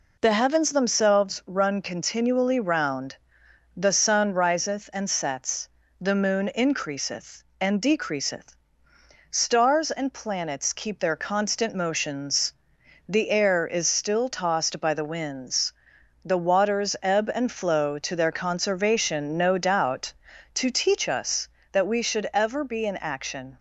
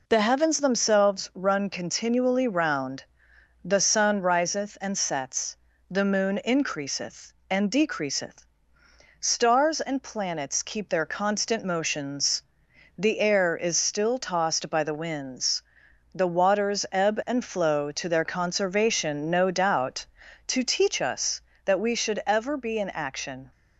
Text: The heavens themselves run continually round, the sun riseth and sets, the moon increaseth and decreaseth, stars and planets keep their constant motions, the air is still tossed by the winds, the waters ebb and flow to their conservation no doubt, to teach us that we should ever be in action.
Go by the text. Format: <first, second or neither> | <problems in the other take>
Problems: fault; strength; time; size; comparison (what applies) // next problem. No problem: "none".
neither | none